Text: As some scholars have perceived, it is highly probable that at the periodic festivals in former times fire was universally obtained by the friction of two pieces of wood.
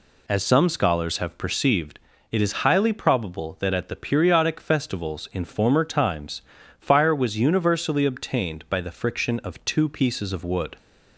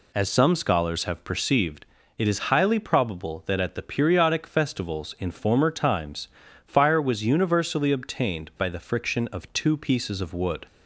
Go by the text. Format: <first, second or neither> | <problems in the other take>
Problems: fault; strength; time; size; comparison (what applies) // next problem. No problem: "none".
neither | pauses between "times" and "fire"; slight; the same in both